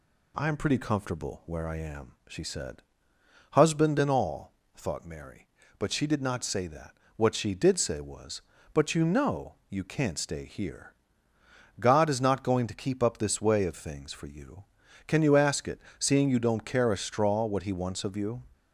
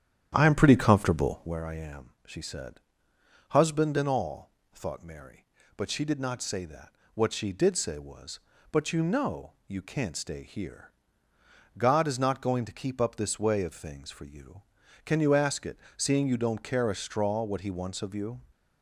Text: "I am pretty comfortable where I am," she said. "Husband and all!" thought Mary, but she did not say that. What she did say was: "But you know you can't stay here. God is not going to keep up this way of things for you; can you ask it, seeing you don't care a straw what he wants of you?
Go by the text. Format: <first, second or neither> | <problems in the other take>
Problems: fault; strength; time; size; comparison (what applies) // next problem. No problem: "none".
first | starts louder than the rest; strong; until 1.6 s; 9.5 dB